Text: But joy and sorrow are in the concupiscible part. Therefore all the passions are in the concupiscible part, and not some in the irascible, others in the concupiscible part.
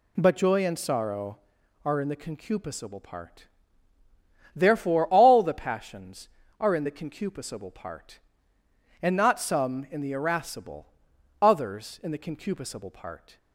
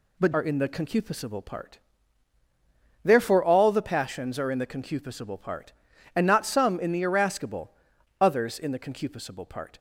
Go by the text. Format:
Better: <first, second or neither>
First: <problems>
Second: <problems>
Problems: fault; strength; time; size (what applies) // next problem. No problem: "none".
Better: first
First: none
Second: skips "joy and sorrow"; at 0.3 s